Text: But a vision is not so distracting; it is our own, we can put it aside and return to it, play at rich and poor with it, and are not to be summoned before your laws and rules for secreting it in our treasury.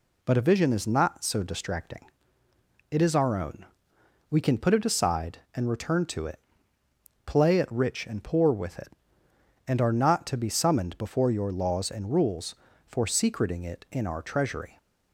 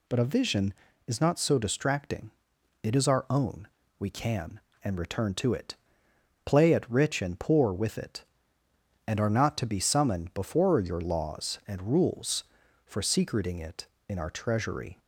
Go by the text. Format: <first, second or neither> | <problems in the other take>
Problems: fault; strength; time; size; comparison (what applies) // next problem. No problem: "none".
first | skips "put it aside"; at 4.7 s